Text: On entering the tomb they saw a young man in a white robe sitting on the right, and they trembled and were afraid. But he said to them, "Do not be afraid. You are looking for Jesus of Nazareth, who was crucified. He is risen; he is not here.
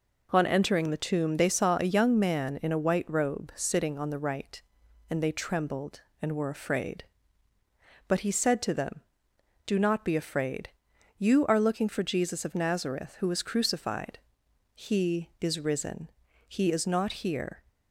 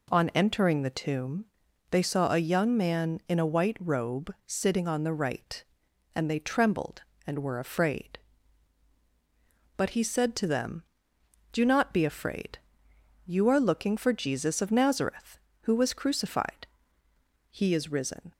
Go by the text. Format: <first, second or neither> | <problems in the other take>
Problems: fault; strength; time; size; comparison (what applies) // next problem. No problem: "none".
first | pauses between "tomb" and "they"; noticeable; at 1.4 s; 0.46 s long // stops before "he is not here"; at 18.3 s